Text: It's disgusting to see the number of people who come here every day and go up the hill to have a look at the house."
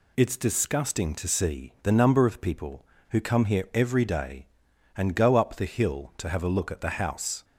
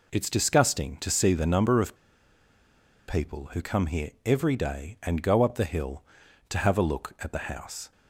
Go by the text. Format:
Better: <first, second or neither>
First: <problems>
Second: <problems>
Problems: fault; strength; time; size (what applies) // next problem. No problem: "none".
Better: first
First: none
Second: pauses between "of" and "people"; at 1.9 s; 1.1 s long // pauses between "here" and "every"; slight; at 4.0 s; 0.16 s long